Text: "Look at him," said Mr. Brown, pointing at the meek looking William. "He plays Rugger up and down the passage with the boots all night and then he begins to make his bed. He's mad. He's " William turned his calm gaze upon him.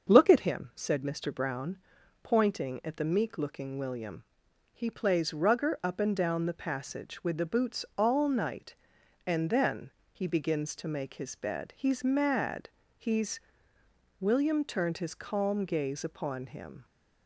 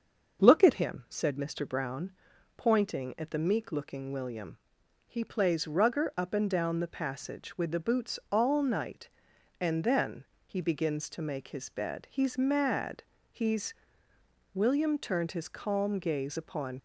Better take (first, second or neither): first